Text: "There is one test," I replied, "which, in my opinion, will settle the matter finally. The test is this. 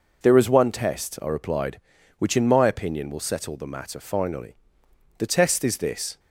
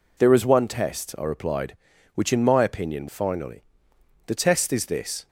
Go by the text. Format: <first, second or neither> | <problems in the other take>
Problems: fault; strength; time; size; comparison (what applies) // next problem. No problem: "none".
first | skips "will settle the matter"; at 3.0 s